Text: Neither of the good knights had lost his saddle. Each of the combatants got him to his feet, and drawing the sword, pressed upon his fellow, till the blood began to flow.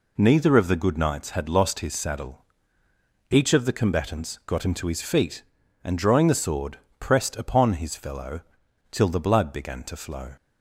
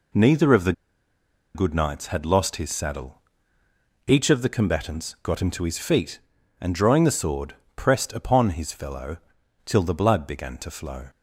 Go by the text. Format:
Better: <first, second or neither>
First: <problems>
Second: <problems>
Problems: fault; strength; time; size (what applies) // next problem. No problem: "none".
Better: first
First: none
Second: pauses between "the" and "good"; noticeable; at 0.7 s; 0.82 s long